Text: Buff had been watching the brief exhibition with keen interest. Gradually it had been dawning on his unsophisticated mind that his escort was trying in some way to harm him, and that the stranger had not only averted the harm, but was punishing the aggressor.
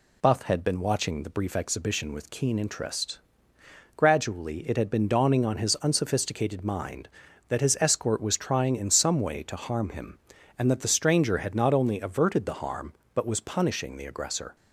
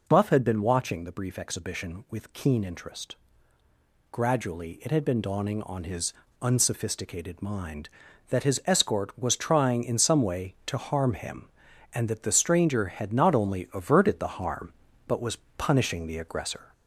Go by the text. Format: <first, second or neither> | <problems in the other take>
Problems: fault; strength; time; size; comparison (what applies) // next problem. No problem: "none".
first | gets louder; throughout; 3.5 dB // pauses between "his" and "unsophisticated"; slight; at 6.1 s; 0.28 s long // pauses between "was" and "punishing"; slight; at 15.3 s; 0.20 s long